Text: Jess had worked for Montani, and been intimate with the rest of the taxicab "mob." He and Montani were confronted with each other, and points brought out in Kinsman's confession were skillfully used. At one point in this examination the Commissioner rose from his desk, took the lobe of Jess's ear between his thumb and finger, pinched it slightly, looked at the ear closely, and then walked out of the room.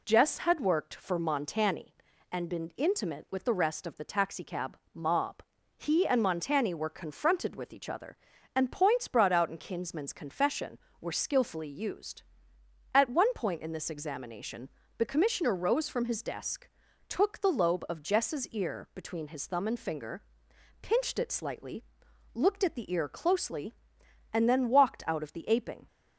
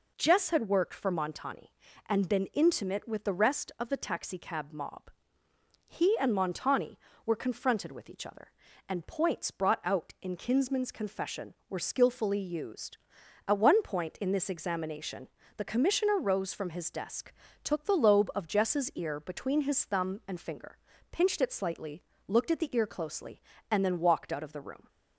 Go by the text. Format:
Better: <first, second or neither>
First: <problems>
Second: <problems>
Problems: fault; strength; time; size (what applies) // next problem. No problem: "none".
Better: second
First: pauses between "taxicab" and "mob"; slight; at 4.7 s; 0.16 s long // pauses between "examination" and "the"; slight; at 14.6 s; 0.30 s long // says "aping" for "room"; at 25.4 s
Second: pauses between "examination" and "the"; slight; at 15.2 s; 0.26 s long